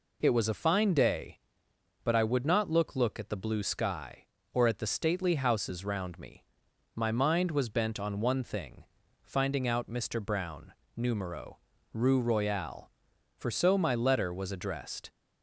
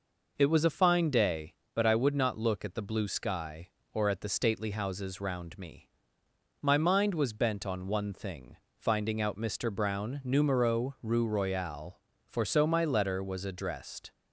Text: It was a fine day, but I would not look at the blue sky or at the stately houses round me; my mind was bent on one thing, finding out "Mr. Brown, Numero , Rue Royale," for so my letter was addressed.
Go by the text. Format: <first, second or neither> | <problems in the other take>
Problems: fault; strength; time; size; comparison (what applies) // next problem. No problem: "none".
second | says "look" twice; at 2.9 s